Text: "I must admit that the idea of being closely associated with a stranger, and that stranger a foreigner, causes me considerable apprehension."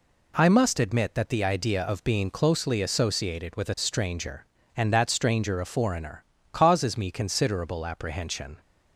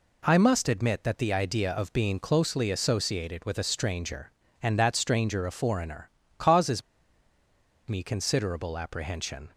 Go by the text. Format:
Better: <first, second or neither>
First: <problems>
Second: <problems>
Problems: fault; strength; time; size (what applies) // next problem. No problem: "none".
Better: first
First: none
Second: pauses between "causes" and "me"; at 6.8 s; 1.0 s long